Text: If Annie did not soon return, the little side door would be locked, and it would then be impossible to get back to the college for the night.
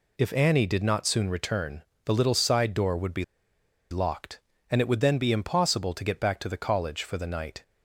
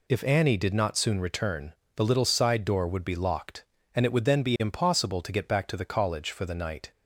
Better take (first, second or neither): second